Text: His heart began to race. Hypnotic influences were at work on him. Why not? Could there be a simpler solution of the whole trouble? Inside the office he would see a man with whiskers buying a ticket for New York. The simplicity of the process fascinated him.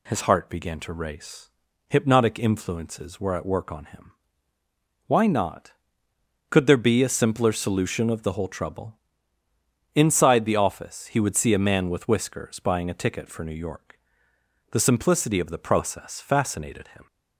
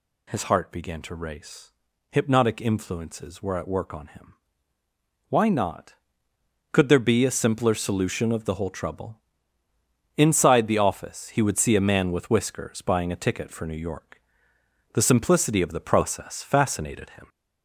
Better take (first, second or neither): first